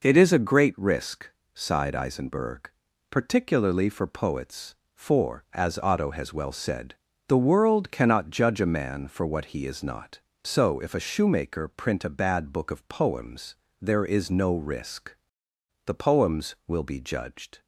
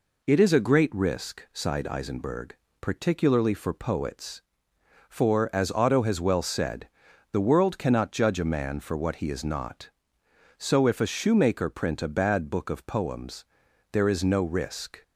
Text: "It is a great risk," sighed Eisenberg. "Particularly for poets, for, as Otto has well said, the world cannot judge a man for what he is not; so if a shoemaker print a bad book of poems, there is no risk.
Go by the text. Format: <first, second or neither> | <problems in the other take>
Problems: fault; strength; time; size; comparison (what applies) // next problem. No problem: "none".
second | goes on to say "The poems will be judged"; strong; from 15.8 s on; 1.7 s long